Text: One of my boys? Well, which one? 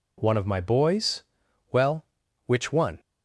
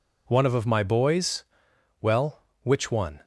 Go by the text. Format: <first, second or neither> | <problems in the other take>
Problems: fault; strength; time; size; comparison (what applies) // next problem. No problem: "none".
first | says "of" twice; at 0.5 s